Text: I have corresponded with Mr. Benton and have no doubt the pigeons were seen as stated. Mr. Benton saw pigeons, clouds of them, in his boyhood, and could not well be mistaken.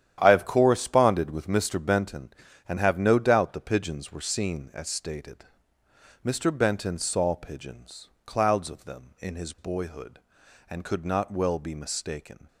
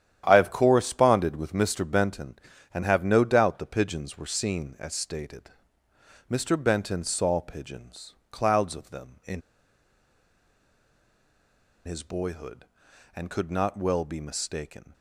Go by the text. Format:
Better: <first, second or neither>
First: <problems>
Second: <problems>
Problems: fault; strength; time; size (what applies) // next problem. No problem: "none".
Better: first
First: starts louder than the rest; strong; until 1.2 s; 10.5 dB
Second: starts louder than the rest; strong; until 1.2 s; 10.5 dB // pauses between "in" and "his"; strong; at 9.4 s; 2.4 s long